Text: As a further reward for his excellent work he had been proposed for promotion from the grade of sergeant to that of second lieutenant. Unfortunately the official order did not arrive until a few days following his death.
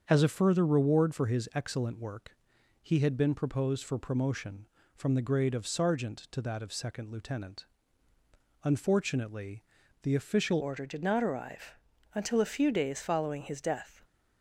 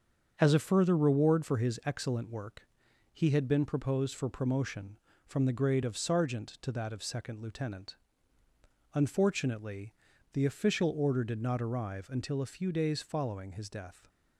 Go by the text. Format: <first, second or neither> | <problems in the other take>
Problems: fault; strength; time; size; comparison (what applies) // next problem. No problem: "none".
second | starts louder than the rest; until 1.0 s; 7 dB; also in the second // pauses between "work" and "he"; noticeable; at 2.3 s; 0.46 s long; noticeable in the second // pauses between "Unfortunately" and "the"; at 9.6 s; 0.40 s long; also in the second // changes voice at "order"; from 10.6 s on; 3.3 s long // pauses between "arrive" and "until"; at 11.7 s; 0.42 s long